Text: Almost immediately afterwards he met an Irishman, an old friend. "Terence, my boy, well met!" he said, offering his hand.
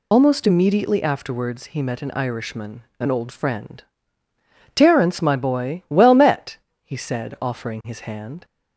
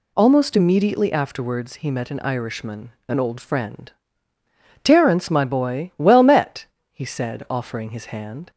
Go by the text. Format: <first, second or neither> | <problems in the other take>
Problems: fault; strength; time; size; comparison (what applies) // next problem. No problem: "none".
second | loses the start of "Almost"; at 0.1 s; 55 ms